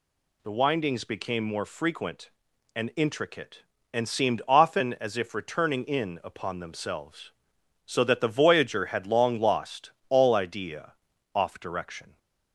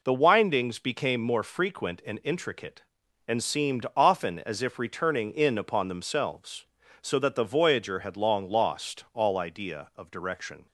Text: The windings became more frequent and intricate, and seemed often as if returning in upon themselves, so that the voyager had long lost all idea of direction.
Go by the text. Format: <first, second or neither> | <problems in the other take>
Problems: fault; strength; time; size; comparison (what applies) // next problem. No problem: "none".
second | pauses between "lost" and "all"; slight; at 9.8 s; 0.20 s long // says "off" for "of"; at 11.3 s